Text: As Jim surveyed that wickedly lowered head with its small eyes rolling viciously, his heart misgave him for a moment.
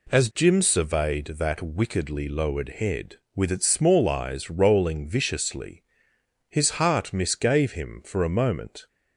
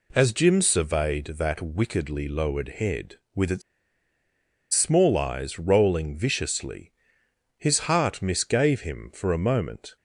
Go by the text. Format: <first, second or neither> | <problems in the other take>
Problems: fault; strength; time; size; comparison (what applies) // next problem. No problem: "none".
first | pauses between "its" and "small"; at 3.6 s; 1.1 s long